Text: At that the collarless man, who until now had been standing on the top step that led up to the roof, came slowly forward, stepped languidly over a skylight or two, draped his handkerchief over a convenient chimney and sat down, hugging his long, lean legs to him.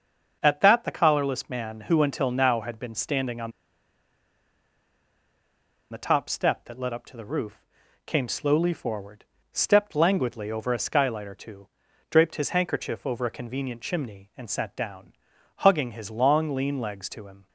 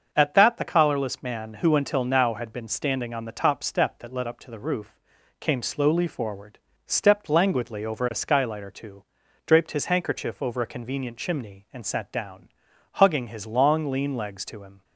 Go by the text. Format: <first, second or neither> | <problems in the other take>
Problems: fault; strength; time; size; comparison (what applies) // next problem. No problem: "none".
second | starts louder than the rest; until 1.4 s; 6.5 dB; also in the second // pauses between "on" and "the"; strong; at 3.5 s; 2.4 s long